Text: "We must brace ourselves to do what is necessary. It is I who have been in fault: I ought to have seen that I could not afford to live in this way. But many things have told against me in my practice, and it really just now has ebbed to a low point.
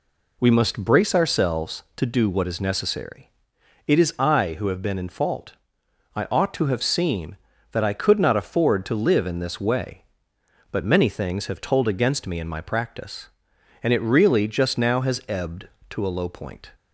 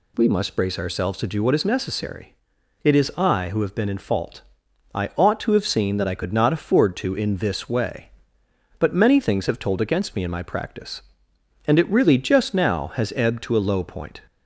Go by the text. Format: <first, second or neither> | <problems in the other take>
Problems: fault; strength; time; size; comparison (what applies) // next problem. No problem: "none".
first | skips "live"; at 7.1 s